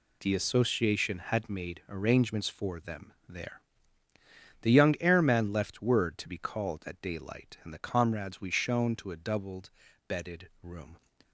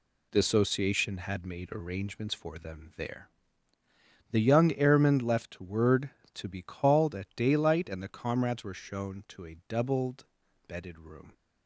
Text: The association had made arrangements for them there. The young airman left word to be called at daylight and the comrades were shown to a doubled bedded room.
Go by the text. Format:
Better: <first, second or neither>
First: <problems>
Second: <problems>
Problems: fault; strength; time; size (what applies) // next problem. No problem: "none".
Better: second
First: pauses between "them" and "there"; slight; at 3.1 s; 0.16 s long // says "we" for "were"; at 8.4 s // pauses between "doubled" and "bedded"; at 9.6 s; 0.40 s long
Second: pauses between "doubled" and "bedded"; at 10.2 s; 0.42 s long